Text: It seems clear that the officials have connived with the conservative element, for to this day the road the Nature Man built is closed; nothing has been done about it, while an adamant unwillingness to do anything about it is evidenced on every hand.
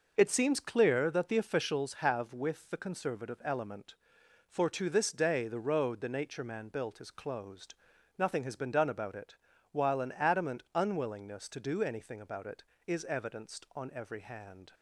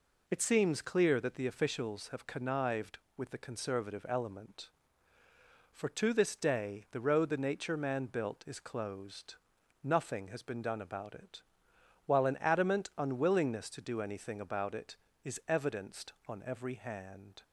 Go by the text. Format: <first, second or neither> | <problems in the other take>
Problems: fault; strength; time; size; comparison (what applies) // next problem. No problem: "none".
second | skips "connived"; at 2.3 s